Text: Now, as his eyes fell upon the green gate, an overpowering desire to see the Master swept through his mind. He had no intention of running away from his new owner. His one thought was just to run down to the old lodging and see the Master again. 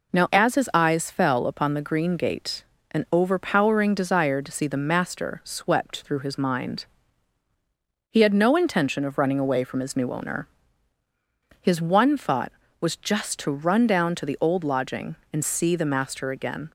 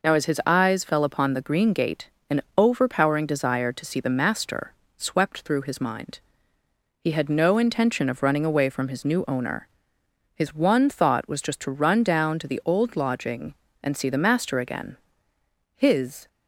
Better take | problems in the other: first | pauses between "an" and "overpowering"; slight; at 2.4 s; 0.16 s long // pauses between "Master" and "swept"; slight; at 4.7 s; 0.22 s long // goes on to say "His"; from 15.7 s on; 0.52 s long

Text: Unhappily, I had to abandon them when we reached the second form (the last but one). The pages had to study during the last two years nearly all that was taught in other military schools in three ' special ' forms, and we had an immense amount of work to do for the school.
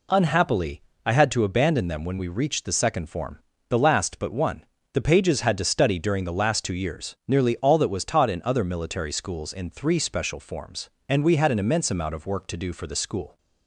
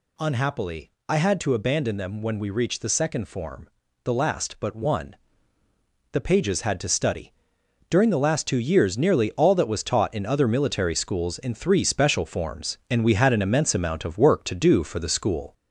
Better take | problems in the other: first | gets louder; slight; throughout; 3.5 dB // pauses between "study" and "during"; noticeable; at 7.3 s; 0.56 s long

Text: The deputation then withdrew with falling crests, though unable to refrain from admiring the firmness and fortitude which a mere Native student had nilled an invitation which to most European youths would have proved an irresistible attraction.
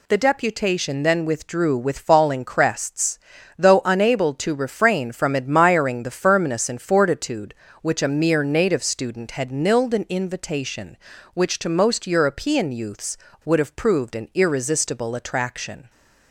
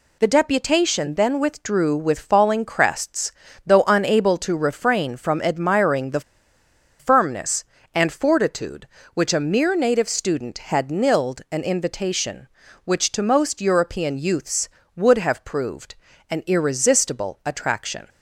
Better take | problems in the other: first | pauses between "the" and "firmness"; noticeable; at 6.2 s; 0.79 s long // pauses between "proved" and "an"; slight; at 15.9 s; 0.34 s long

